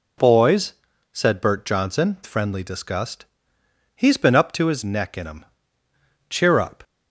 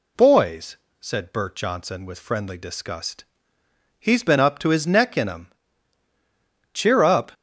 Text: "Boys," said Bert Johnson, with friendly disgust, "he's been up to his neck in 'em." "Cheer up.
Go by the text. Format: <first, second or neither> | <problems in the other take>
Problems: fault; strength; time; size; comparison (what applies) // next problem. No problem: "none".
second | skips "with"; at 2.2 s